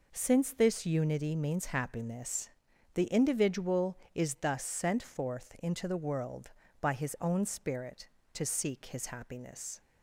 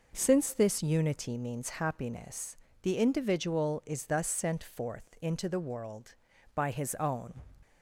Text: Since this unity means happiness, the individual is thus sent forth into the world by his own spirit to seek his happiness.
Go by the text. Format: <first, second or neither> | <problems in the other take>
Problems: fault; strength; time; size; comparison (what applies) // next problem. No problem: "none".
first | stops before "spirit to seek his happiness"; at 7.6 s